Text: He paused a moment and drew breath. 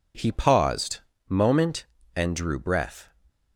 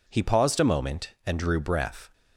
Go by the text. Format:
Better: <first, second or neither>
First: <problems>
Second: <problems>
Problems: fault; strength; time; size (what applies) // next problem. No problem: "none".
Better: second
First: skips "a"; at 1.1 s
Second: none